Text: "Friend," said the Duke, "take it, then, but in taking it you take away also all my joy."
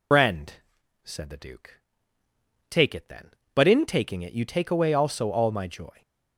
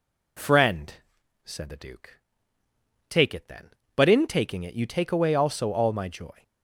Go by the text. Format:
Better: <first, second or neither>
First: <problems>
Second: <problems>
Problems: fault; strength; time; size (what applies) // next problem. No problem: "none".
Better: second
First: loses the start of "Friend"; at 0.1 s; 150 ms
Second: none